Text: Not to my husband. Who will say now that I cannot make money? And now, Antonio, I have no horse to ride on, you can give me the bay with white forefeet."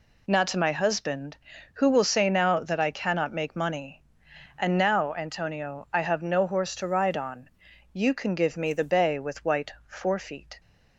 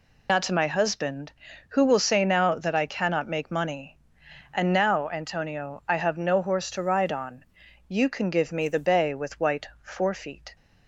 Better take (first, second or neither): first